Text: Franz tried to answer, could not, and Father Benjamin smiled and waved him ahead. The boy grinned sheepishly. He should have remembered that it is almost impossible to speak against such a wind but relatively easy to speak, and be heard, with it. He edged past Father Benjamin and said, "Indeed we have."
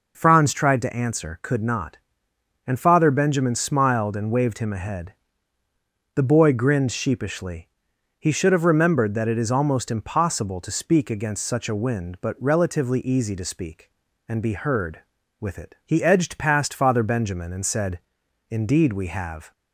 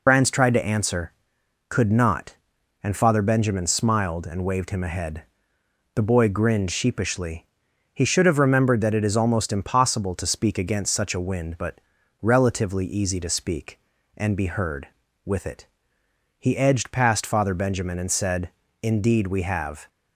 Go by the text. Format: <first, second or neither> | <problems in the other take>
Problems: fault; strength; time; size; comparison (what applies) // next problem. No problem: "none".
first | loses the start of "Franz"; at 0.0 s; 95 ms // pauses between "but" and "relatively"; at 11.7 s; 0.42 s long